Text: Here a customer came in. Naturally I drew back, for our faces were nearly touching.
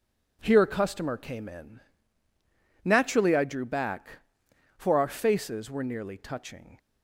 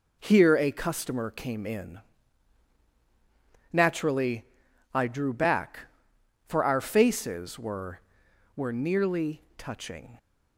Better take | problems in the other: first | pauses between "Naturally" and "I"; noticeable; at 4.4 s; 0.50 s long // says "were" twice; at 8.5 s

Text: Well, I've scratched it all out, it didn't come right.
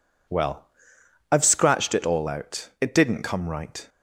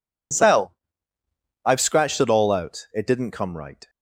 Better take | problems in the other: first | says "Cell" for "Well"; at 0.3 s

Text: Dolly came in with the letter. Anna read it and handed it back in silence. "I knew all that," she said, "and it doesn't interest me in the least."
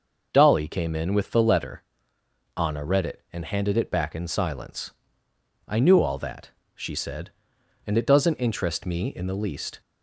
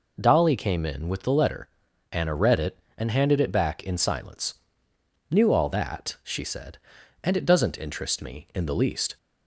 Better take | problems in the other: first | skips "I"; at 4.9 s

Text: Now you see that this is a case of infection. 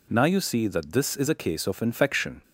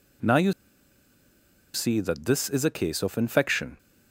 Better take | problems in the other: first | pauses between "you" and "see"; at 0.5 s; 1.2 s long

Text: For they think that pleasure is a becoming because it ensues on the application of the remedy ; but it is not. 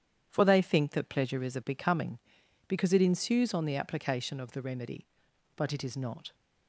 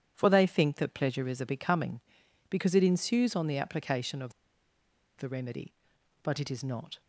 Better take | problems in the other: first | starts louder than the rest; strong; until 1.1 s; 10 dB; strong in the first // pauses between "of" and "the"; noticeable; at 4.3 s; 0.86 s long

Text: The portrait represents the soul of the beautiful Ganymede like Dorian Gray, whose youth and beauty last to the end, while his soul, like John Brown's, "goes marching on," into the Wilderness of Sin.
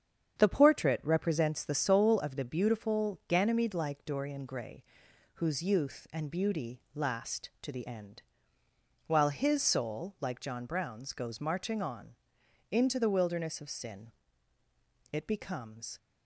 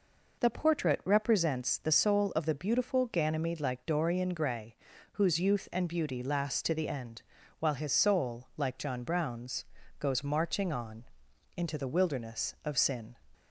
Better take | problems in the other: second | starts louder than the rest; strong; until 1.4 s; 8 dB // goes on to say "It becomes"; noticeable; from 15.1 s on; 0.86 s long

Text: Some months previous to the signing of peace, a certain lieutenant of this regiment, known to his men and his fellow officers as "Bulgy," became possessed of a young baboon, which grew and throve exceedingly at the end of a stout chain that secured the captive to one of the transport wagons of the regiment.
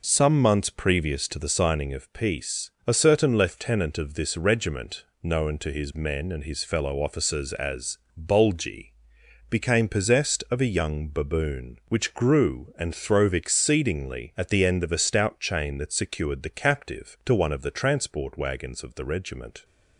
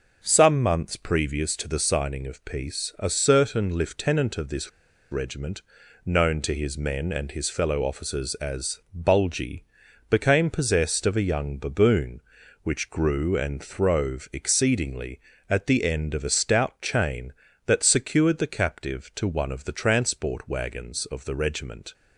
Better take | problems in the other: first | pauses between "this" and "regiment"; at 4.6 s; 0.41 s long // pauses between "as" and "Bulgy"; slight; at 8.7 s; 0.16 s long; slight in the first

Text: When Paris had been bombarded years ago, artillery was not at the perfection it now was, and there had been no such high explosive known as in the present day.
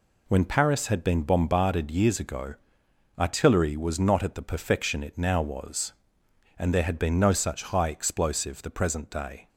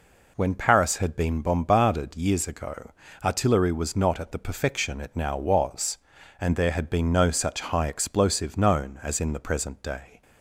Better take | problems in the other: second | skips "known as in"; at 8.6 s

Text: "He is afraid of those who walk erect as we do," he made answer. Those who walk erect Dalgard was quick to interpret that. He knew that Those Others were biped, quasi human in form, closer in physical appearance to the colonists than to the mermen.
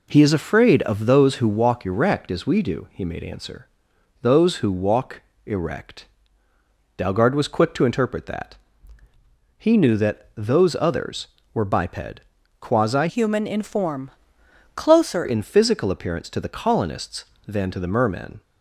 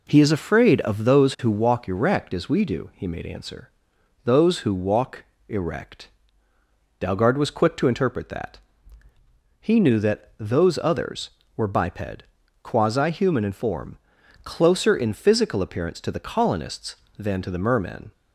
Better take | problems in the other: second | pauses between "walk" and "erect"; slight; at 5.2 s; 0.24 s long; slight in the second // pauses between "erect" and "Dalgard"; noticeable; at 6.0 s; 0.90 s long; noticeable in the second // changes voice from "human" to "closer"; from 13.0 to 15.2 s; 2.2 s long

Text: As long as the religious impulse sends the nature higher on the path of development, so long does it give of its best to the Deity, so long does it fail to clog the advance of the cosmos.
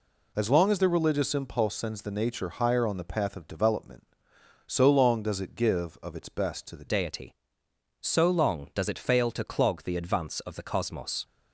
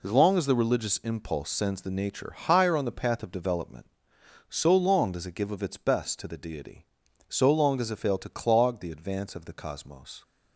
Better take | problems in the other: second | changes voice at "Deity"; from 6.8 s on; 4.4 s long

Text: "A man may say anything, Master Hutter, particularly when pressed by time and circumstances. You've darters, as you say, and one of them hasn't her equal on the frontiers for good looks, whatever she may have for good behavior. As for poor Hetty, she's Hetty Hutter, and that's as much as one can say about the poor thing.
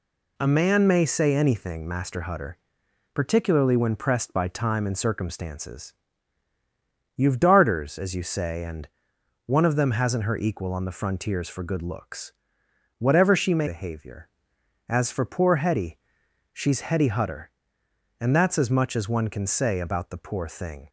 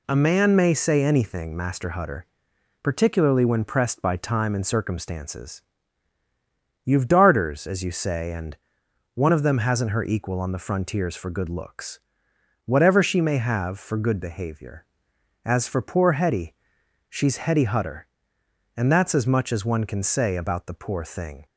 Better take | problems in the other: second | pauses between "and" and "one"; noticeable; at 8.8 s; 0.60 s long; noticeable in the second // skips "have for good"; at 13.6 s

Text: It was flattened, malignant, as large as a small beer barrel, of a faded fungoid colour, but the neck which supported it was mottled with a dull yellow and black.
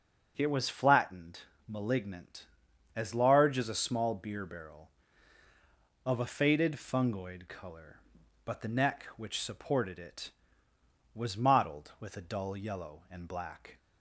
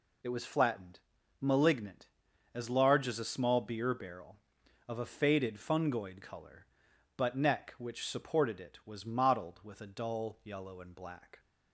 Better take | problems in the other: first | skips "the"; at 7.3 s

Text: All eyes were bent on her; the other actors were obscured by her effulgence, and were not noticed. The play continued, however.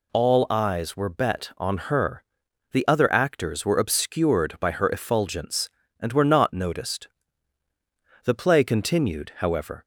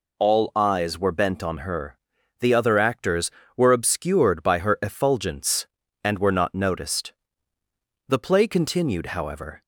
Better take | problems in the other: second | says "bet" for "bent"; at 1.0 s

